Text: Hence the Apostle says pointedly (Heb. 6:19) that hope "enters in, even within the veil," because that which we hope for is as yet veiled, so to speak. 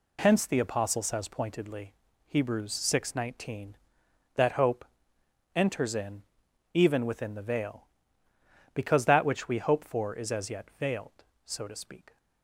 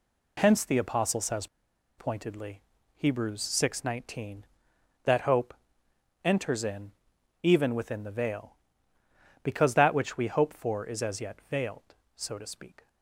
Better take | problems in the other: first | pauses between "says" and "pointedly"; noticeable; at 1.4 s; 0.49 s long // pauses between "hope" and "enters"; noticeable; at 5.5 s; 0.72 s long; noticeable in the first

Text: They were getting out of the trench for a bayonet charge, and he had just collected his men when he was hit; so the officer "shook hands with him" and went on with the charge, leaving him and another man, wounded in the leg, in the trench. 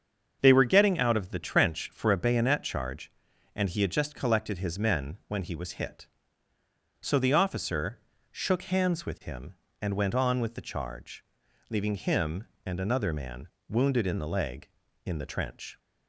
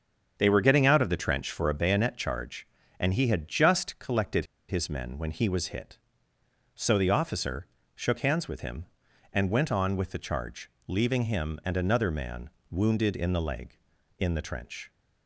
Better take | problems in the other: first | starts louder than the rest; strong; until 1.3 s; 7.5 dB; also in the first // pauses between "collected" and "his"; slight; at 4.4 s; 0.24 s long // pauses between "officer" and "shook"; slight; at 7.6 s; 0.28 s long; slight in the first

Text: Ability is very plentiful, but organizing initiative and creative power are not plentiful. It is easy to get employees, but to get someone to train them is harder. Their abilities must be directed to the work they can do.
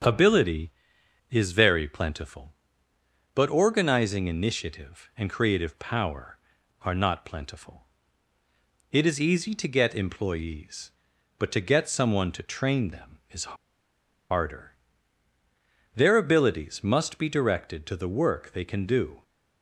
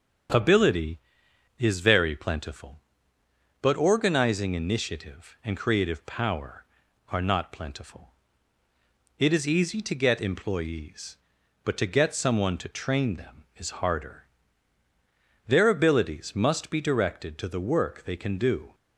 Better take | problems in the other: second | starts louder than the rest; until 1.6 s; 7 dB; also in the second // pauses between "is" and "harder"; noticeable; at 13.5 s; 0.75 s long

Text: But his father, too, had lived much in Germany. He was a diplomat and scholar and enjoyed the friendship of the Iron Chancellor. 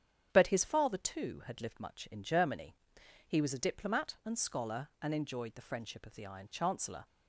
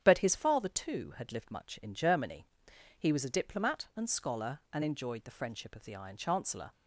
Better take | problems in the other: neither | starts louder than the rest; strong; the same in both

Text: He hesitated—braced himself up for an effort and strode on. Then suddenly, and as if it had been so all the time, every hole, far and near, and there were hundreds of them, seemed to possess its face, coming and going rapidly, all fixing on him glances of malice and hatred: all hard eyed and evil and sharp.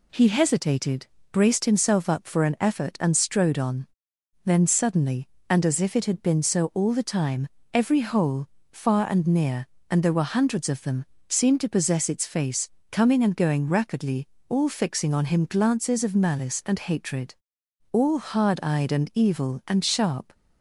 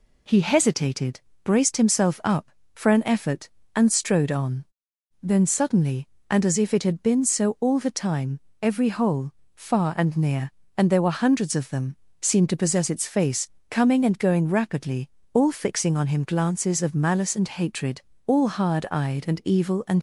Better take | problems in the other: first | stops before "sharp"; at 19.9 s

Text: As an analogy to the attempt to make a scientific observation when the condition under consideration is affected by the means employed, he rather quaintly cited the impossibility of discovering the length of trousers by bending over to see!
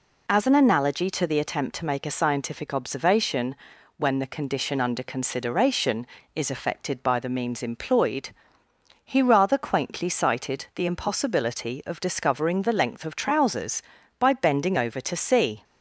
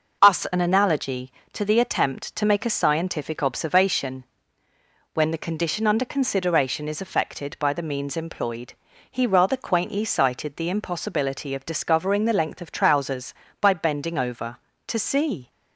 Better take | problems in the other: first | says "Us" for "As"; at 0.2 s // pauses between "observation" and "when"; noticeable; at 4.2 s; 0.90 s long; also in the first

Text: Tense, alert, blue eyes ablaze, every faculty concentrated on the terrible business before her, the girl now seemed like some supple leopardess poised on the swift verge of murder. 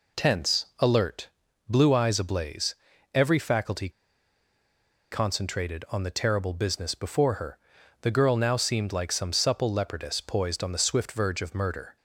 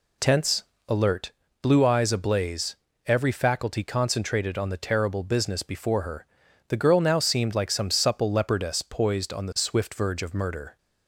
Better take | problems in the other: second | pauses between "faculty" and "concentrated"; at 3.8 s; 1.2 s long

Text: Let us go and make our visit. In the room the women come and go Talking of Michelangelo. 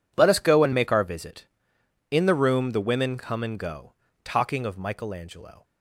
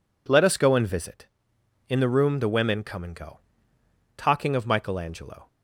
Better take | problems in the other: first | skips "make our"; at 0.8 s // pauses between "go" and "Talking"; noticeable; at 3.3 s; 0.78 s long; slight in the first

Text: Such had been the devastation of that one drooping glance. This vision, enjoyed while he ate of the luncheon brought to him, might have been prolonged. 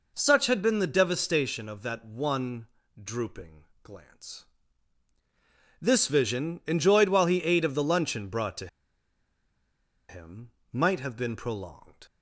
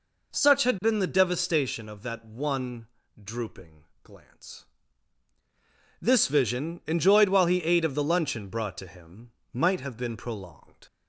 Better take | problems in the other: second | pauses between "one" and "drooping"; slight; at 2.6 s; 0.34 s long; slight in the second // pauses between "drooping" and "glance"; slight; at 3.6 s; 0.18 s long; slight in the second // pauses between "to" and "him"; strong; at 8.6 s; 1.4 s long

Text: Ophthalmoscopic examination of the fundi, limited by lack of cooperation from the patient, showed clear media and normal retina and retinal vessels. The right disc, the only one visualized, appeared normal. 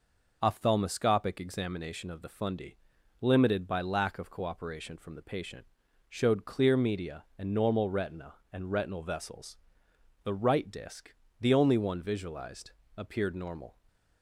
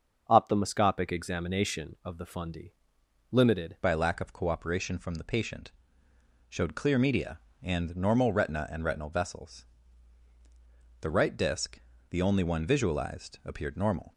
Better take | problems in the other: first | starts louder than the rest; until 1.3 s; 6.5 dB // changes voice at "by"; from 3.8 s on; 10.3 s long

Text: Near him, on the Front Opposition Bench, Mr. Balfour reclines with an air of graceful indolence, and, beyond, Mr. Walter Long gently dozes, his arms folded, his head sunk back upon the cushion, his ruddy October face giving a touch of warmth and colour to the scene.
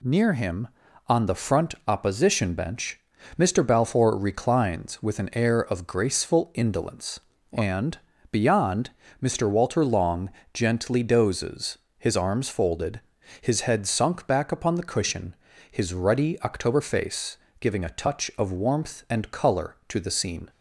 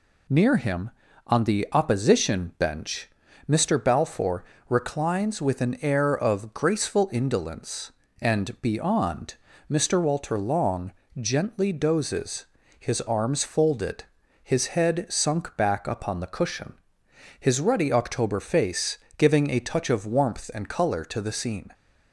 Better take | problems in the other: first | skips "Front"; at 1.6 s // pauses between "Balfour" and "reclines"; slight; at 4.4 s; 0.26 s long // pauses between "Long" and "gently"; slight; at 10.9 s; 0.26 s long; slight in the first // pauses between "face" and "giving"; slight; at 18.9 s; 0.20 s long; slight in the first

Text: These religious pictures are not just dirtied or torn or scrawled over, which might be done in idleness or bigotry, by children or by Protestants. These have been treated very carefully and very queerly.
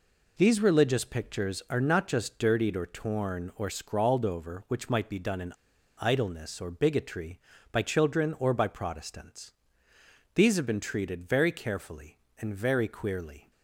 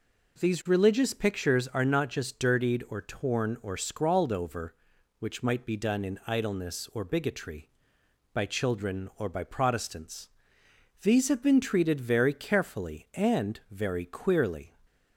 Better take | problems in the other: second | pauses between "in" and "idleness"; noticeable; at 5.5 s; 0.47 s long

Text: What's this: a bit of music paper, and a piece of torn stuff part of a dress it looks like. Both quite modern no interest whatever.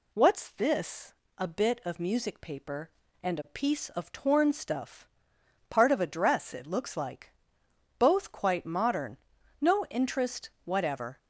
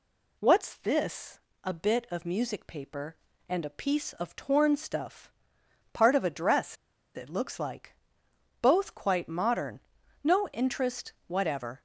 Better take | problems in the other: first | pauses between "stuff" and "part"; noticeable; at 5.3 s; 0.62 s long; noticeable in the first // pauses between "dress" and "it"; at 6.7 s; 0.40 s long // pauses between "modern" and "no"; at 9.8 s; 0.42 s long; also in the first

